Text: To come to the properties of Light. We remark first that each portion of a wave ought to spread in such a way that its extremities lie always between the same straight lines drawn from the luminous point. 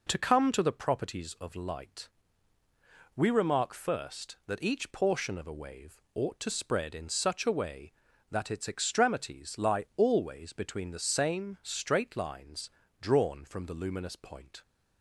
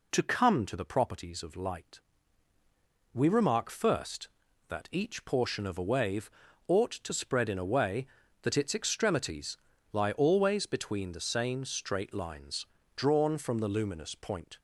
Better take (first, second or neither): first